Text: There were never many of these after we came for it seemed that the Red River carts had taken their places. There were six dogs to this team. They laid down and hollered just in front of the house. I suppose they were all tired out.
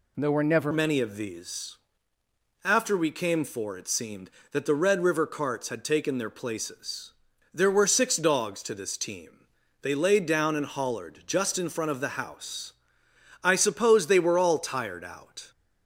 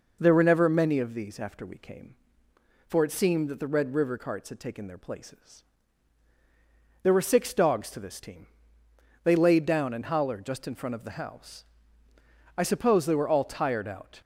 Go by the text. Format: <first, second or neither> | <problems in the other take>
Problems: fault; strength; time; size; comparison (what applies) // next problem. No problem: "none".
second | changes voice at "many"; from 0.7 s on; 14.8 s long // pauses between "these" and "after"; noticeable; at 1.7 s; 0.86 s long